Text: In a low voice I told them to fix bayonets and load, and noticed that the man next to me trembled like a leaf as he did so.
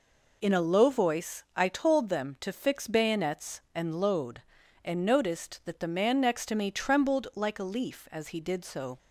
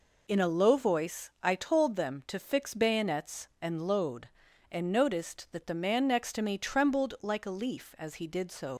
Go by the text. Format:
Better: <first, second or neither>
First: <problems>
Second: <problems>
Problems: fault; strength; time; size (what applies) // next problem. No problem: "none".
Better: first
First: none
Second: leaves "so" unfinished; at 8.7 s; 75 ms